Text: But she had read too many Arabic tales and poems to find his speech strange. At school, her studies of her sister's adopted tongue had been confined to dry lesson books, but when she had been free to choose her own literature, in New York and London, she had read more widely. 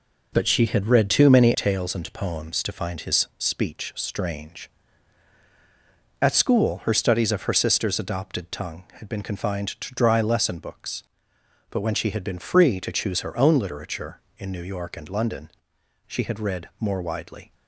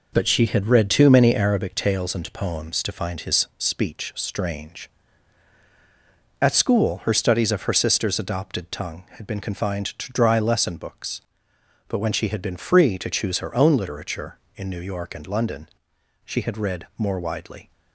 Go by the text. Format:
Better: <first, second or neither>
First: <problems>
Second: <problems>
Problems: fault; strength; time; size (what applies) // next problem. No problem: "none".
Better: second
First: skips "Arabic"; at 1.5 s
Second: none